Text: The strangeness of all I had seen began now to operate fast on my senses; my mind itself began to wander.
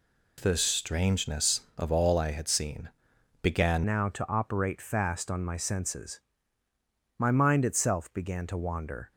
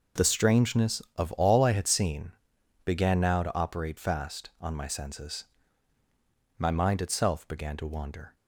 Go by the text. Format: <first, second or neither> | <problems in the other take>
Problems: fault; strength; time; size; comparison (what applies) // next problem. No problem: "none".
second | pauses between "seen" and "began"; noticeable; at 2.8 s; 0.54 s long; noticeable in the second // changes voice at "now"; from 3.8 s on; 5.3 s long